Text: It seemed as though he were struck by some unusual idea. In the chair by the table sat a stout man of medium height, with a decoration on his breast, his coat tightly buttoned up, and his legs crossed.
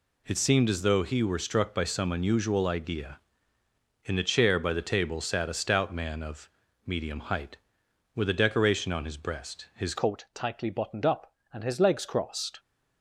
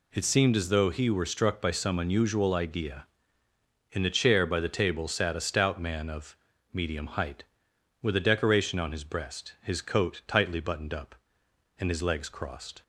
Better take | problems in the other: second | pauses between "of" and "medium"; slight; at 6.4 s; 0.36 s long; slight in the second // changes voice at "coat"; from 9.9 s on; 2.6 s long

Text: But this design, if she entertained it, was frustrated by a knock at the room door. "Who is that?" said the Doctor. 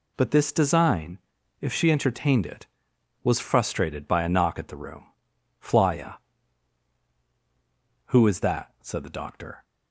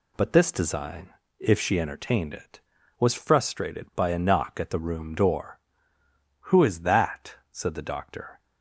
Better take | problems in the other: second | says "flya" for "door"; at 5.5 s

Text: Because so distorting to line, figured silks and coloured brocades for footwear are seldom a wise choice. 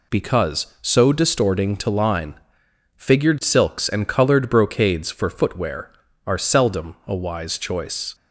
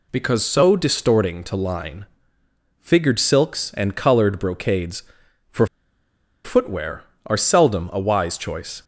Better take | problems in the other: first | pauses between "for" and "footwear"; noticeable; at 5.6 s; 0.77 s long

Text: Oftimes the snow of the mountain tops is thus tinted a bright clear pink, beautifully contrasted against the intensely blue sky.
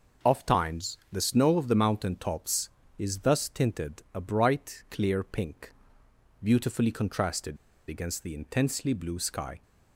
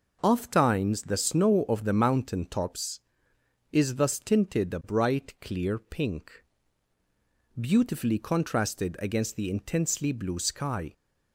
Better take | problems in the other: second | pauses between "contrasted" and "against"; slight; at 7.5 s; 0.31 s long

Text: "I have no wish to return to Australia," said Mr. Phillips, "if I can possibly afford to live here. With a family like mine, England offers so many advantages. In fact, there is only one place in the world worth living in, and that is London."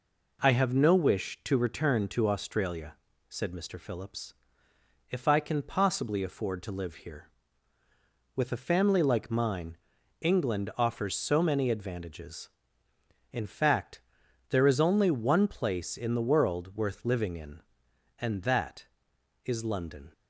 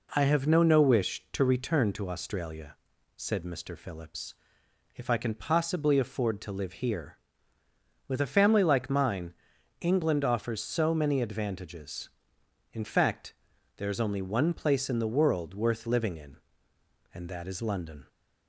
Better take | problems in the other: first | says "no" twice; at 0.6 s

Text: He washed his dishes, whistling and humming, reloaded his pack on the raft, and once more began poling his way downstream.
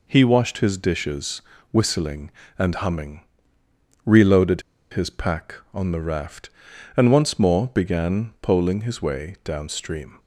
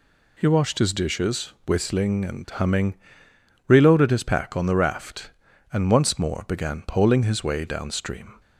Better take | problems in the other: second | pauses between "reloaded" and "his"; slight; at 4.6 s; 0.29 s long

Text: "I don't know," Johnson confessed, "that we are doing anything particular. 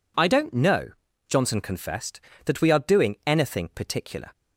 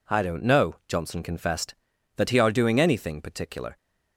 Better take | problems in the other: first | says "he" for "we"; at 2.2 s

